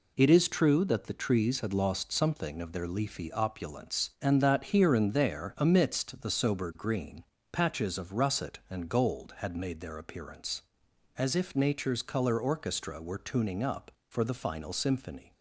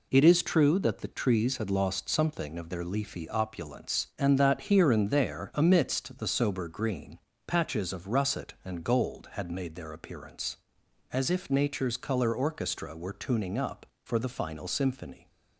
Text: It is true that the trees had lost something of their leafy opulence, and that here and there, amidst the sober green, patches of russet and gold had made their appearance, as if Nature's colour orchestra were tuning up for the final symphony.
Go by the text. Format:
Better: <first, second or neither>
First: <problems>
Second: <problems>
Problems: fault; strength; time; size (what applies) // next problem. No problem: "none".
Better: neither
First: none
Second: none